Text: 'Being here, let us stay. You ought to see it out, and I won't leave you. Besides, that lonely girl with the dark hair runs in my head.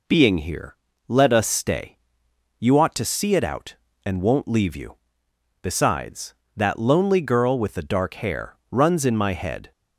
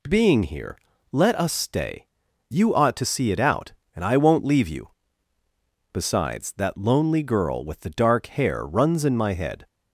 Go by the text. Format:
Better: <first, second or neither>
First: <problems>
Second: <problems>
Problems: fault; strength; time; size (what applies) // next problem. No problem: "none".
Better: second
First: skips "I"; at 4.2 s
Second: none